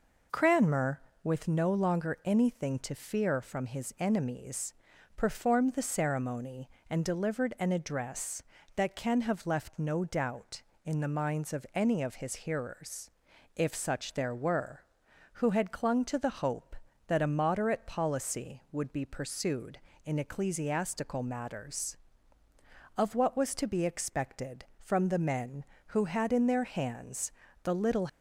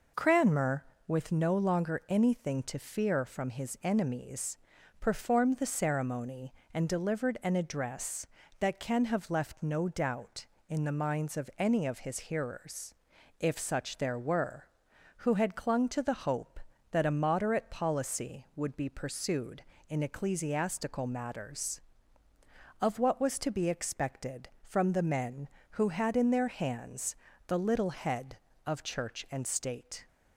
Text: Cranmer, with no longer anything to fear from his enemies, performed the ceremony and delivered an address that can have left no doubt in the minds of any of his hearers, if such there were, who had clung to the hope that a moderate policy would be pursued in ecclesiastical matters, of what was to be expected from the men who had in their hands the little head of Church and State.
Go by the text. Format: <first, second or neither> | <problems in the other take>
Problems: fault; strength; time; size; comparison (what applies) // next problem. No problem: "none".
second | pauses between "hands" and "the"; slight; at 27.3 s; 0.32 s long; slight in the second // stops before "head of Church and State"; at 28.0 s